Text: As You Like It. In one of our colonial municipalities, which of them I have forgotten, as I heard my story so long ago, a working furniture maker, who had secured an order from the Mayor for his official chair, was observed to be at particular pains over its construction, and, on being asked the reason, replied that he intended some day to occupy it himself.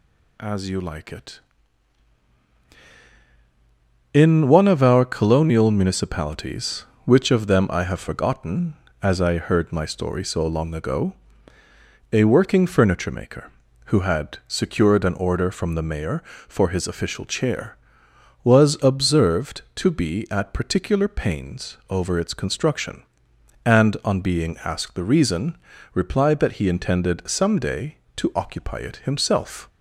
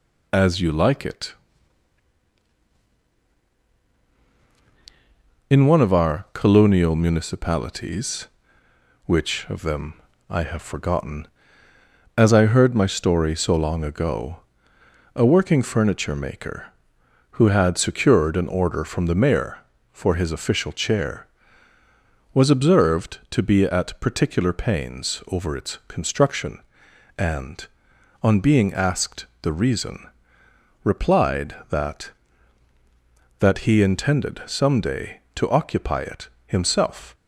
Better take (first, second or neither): first